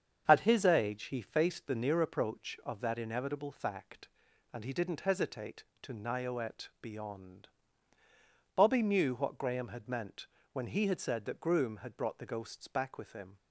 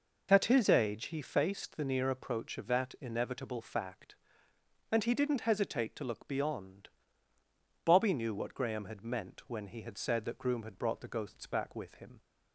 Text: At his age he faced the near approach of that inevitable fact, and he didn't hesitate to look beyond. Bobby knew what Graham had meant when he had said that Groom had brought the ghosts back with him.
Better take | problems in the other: second | starts louder than the rest; strong; until 1.2 s; 7.5 dB // says "nioet" for "look"; at 5.9 s // pauses between "meant" and "when"; slight; at 10.2 s; 0.26 s long

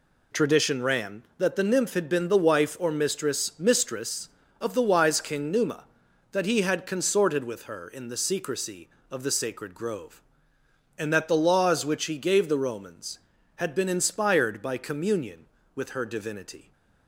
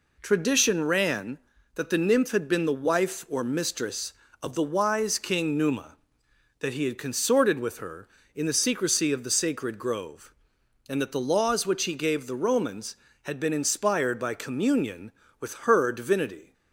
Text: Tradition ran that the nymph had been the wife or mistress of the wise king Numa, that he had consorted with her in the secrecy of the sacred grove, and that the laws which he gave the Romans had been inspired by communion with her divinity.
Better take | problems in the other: second | says "mistress" twice; at 3.5 s

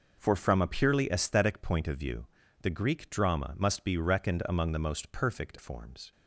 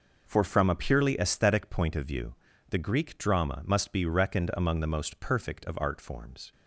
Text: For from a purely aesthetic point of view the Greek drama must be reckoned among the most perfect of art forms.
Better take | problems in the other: second | pauses between "view" and "the"; slight; at 2.2 s; 0.34 s long; slight in the second // skips "of art"; at 5.5 s

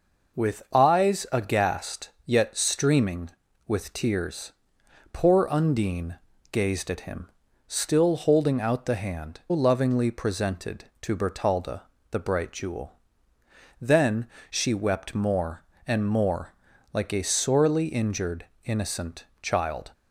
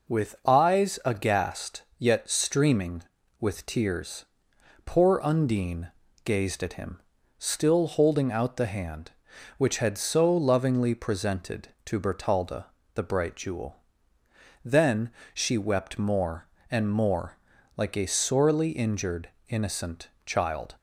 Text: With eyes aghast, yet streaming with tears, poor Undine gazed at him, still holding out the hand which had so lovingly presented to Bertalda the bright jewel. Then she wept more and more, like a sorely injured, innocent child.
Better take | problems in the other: second | pauses between "Undine" and "gazed"; slight; at 6.1 s; 0.34 s long; slight in the second // skips "which had so"; at 9.4 s // pauses between "Bertalda" and "the"; slight; at 11.8 s; 0.26 s long; slight in the second // pauses between "Then" and "she"; slight; at 14.2 s; 0.24 s long; slight in the second // pauses between "innocent" and "child"; slight; at 19.2 s; 0.18 s long; slight in the second

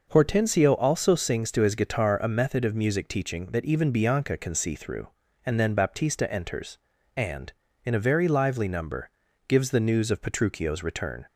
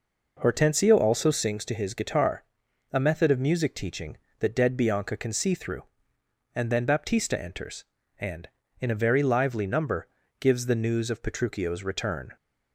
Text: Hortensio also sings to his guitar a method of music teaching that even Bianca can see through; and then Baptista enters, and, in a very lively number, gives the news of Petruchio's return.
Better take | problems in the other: first | pauses between "guitar" and "a"; noticeable; at 2.4 s; 0.48 s long // says "dead" for "even"; at 4.5 s

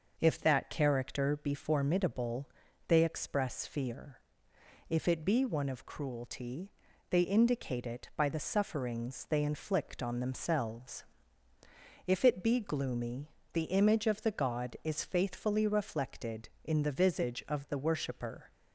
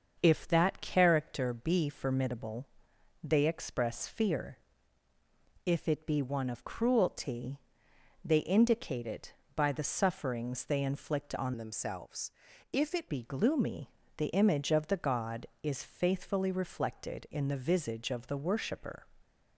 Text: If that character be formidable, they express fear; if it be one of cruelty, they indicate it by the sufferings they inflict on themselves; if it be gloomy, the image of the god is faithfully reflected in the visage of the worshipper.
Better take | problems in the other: first | starts louder than the rest; until 1.2 s; 6.5 dB // changes voice from "themselves" to "it"; from 11.5 to 13.0 s; 1.5 s long

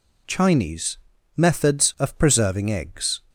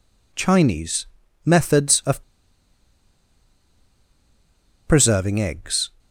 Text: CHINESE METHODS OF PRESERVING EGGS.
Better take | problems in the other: first | pauses between "CHINESE" and "METHODS"; at 1.0 s; 0.38 s long; also in the first // pauses between "OF" and "PRESERVING"; strong; at 2.2 s; 2.6 s long

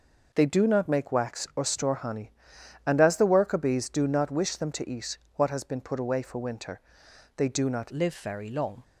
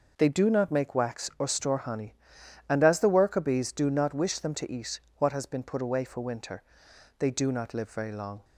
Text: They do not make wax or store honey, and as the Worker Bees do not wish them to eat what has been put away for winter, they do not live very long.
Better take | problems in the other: second | pauses between "eat" and "what"; slight; at 5.1 s; 0.18 s long; slight in the second // changes voice at "live"; from 7.9 s on; 0.9 s long

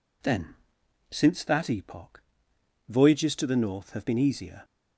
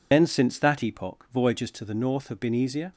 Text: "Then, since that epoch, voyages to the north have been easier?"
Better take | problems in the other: first | loses the start of "Then"; at 0.1 s; 80 ms

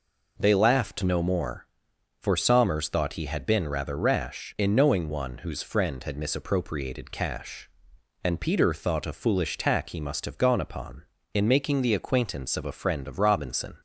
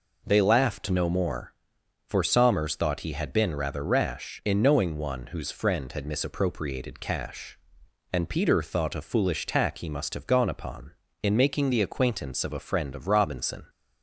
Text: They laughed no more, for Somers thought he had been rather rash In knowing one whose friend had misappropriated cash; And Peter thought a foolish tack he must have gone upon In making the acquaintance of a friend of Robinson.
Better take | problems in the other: neither | none

